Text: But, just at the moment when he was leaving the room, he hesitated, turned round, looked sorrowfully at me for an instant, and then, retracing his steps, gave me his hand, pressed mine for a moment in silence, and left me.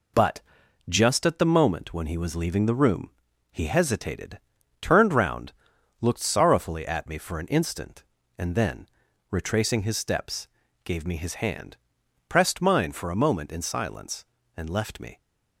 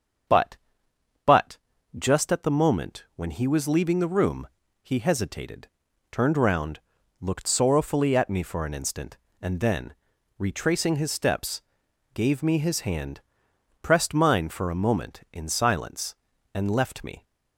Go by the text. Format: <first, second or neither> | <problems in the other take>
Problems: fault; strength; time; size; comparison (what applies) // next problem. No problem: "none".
first | starts louder than the rest; until 2.3 s; 7 dB // says "But" twice; at 1.2 s